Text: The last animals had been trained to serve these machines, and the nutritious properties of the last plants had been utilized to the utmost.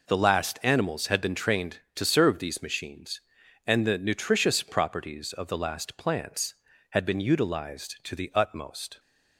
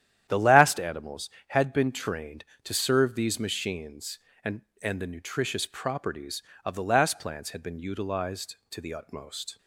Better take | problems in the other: first | starts louder than the rest; strong; until 1.3 s; 10.5 dB // says "and" twice; at 4.8 s

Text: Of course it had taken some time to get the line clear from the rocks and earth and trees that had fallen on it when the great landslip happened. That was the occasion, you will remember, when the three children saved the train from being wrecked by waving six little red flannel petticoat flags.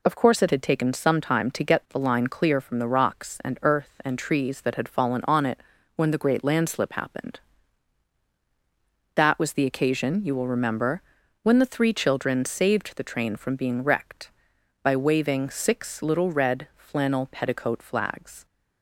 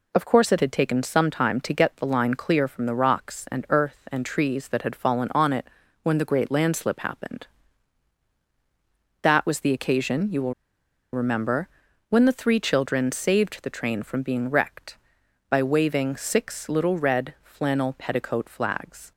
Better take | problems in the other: first | pauses between "it" and "when"; slight; at 5.6 s; 0.36 s long; slight in the first // pauses between "will" and "remember"; noticeable; at 10.5 s; 0.60 s long

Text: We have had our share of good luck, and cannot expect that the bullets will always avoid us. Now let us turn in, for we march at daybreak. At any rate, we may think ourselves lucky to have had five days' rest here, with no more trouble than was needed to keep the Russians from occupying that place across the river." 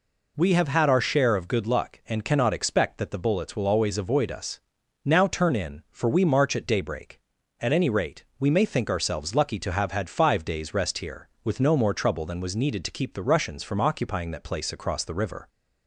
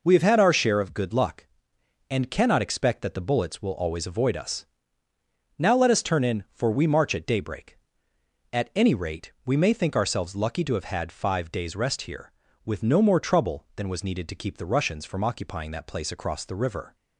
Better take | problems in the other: second | skips "let us"; at 5.2 s

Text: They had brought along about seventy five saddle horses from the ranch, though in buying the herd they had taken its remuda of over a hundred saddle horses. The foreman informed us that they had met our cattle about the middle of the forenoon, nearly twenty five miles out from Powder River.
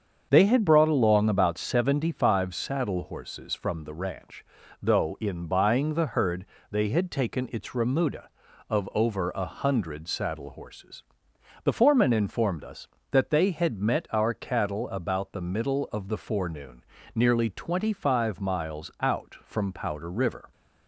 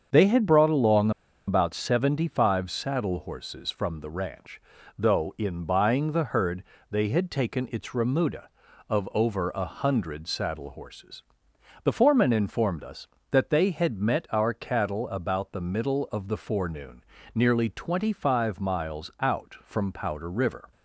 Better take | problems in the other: first | starts louder than the rest; until 1.5 s; 7 dB; also in the first // pauses between "along" and "about"; at 1.1 s; 0.37 s long // pauses between "herd" and "they"; slight; at 6.6 s; 0.26 s long; slight in the first

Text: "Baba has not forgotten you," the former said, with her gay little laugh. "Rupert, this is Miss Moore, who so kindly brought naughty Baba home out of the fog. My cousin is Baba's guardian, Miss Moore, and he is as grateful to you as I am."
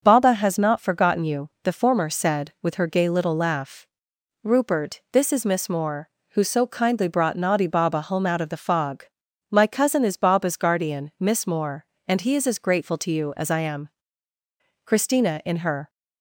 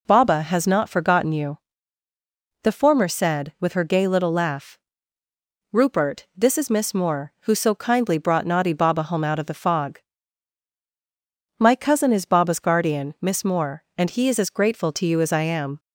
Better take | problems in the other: second | goes on to say "Christina in her"; noticeable; from 14.8 s on; 1.0 s long

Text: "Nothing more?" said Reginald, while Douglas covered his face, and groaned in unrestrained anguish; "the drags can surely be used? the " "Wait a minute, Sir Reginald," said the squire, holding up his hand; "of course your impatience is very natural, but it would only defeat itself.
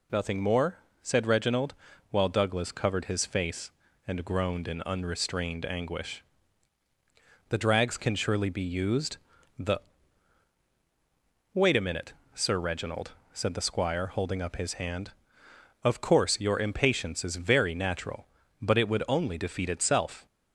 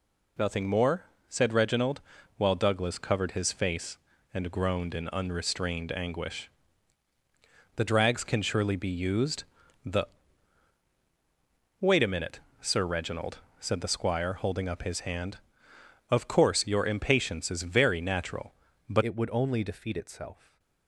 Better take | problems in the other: first | changes voice at "it"; from 19.0 s on; 1.5 s long // stays silent after the last word; slight; from 20.3 s on; 0.5 s long

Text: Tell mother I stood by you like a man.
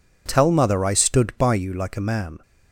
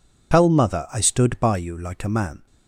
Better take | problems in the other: first | loses the start of "Tell"; at 0.3 s; 65 ms

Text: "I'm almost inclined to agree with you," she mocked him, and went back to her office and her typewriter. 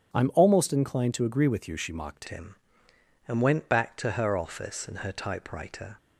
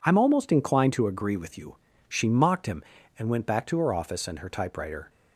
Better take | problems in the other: second | starts louder than the rest; strong; until 1.1 s; 8.5 dB // changes voice at "him"; from 2.2 s on; 3.7 s long

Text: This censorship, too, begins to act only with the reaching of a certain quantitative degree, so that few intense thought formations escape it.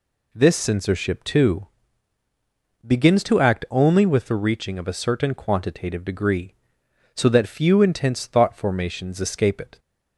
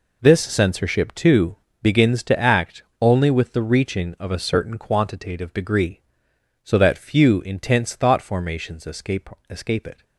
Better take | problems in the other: first | pauses between "act" and "only"; slight; at 2.8 s; 0.16 s long // says "escape" twice; at 9.4 s

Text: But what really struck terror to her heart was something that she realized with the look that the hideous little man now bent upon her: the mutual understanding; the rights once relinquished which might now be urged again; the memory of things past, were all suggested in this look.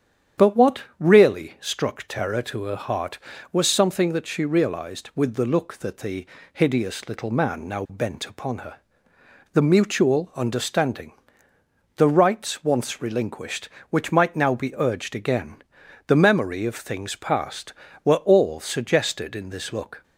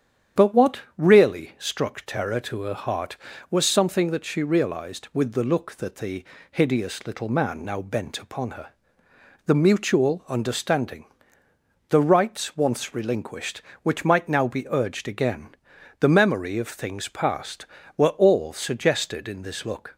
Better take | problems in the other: neither | starts louder than the rest; strong; the same in both // pauses between "what" and "really"; slight; the same in both // pauses between "the" and "hideous"; slight; the same in both

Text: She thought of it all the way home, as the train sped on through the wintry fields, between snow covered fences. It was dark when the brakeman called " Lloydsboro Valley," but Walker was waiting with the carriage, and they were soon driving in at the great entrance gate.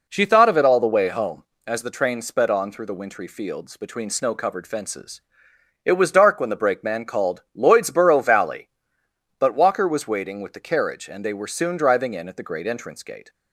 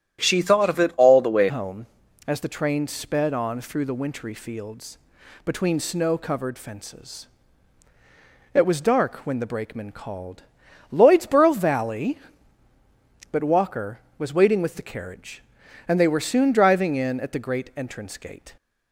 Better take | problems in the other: first | starts louder than the rest; strong; until 1.2 s; 10.5 dB // changes voice at "home"; from 1.4 s on; 17.1 s long

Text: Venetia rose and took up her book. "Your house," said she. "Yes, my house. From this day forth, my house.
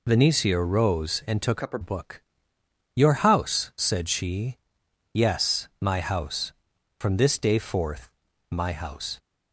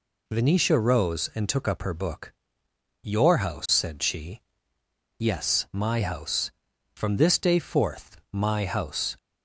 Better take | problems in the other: second | changes voice from "up" to "her"; from 1.6 to 1.8 s; 0.2 s long

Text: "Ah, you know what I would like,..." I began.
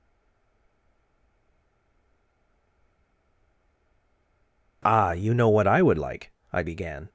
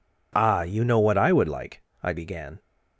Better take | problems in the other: second | stays silent before the first word; strong; until 4.8 s; 4.8 s long

